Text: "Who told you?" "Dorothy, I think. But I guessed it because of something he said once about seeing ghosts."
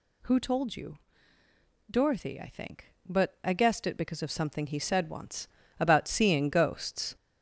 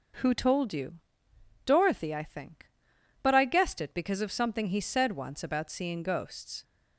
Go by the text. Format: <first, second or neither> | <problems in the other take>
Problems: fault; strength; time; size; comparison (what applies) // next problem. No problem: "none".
second | gets louder; noticeable; throughout; 6 dB // pauses between "once" and "about"; slight; at 5.4 s; 0.32 s long